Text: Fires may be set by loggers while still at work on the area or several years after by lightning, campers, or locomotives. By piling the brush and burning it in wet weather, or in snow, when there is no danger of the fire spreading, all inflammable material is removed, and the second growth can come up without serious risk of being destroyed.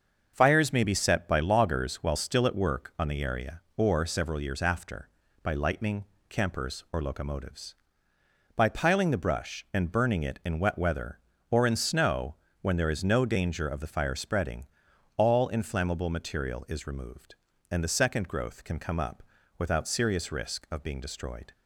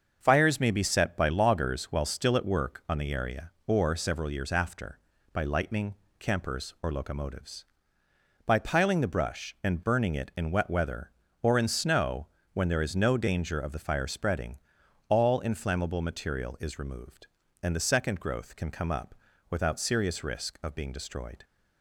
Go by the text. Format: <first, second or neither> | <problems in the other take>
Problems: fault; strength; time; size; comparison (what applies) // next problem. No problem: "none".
neither | starts louder than the rest; the same in both // pauses between "up" and "without"; slight; the same in both